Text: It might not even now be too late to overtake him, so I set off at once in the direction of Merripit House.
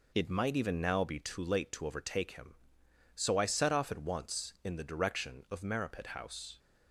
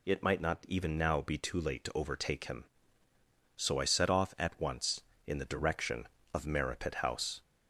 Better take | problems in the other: second | skips "not"; at 0.5 s

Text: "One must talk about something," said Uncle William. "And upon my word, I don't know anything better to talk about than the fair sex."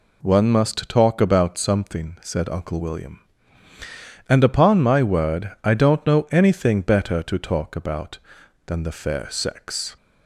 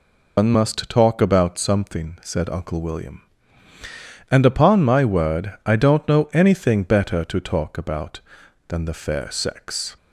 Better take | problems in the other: first | loses the start of "One"; at 0.3 s; 150 ms

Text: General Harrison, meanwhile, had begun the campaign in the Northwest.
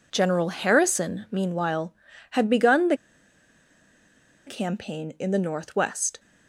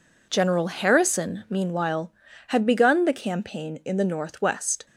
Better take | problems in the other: second | pauses between "the" and "campaign"; strong; at 2.9 s; 1.5 s long

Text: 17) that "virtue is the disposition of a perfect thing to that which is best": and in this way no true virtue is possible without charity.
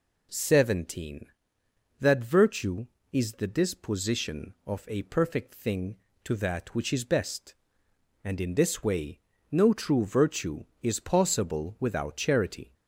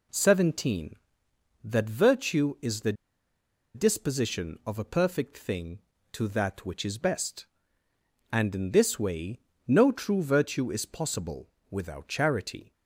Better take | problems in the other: first | pauses between "the" and "disposition"; noticeable; at 2.9 s; 0.81 s long // pauses between "way" and "no"; slight; at 9.3 s; 0.28 s long; slight in the first // pauses between "possible" and "without"; slight; at 11.4 s; 0.24 s long

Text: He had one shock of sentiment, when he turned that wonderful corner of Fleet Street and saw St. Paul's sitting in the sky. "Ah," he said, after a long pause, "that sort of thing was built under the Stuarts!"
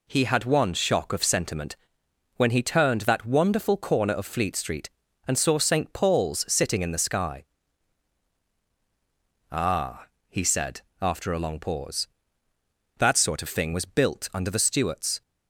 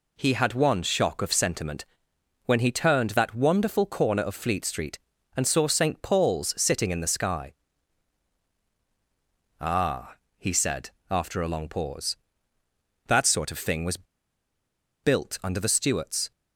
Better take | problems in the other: first | pauses between "was" and "built"; at 14.0 s; 0.98 s long

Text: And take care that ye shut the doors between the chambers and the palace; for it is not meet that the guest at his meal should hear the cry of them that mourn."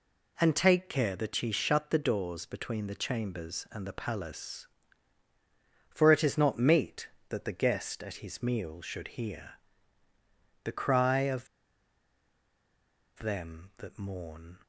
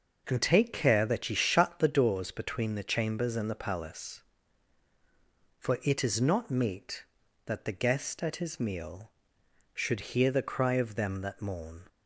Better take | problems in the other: second | pauses between "hear" and "the"; at 9.5 s; 1.1 s long // pauses between "of" and "them"; strong; at 11.4 s; 1.7 s long

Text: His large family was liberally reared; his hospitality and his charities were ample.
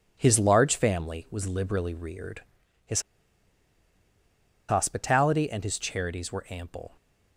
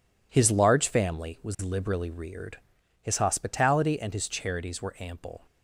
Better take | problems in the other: second | pauses between "his" and "hospitality"; strong; at 3.0 s; 1.6 s long

